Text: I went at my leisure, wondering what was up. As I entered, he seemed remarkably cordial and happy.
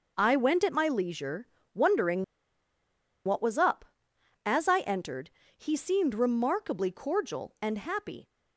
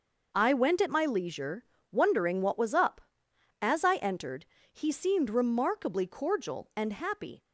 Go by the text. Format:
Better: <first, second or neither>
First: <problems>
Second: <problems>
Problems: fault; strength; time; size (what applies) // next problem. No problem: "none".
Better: second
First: pauses between "wondering" and "what"; at 2.2 s; 1.0 s long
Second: none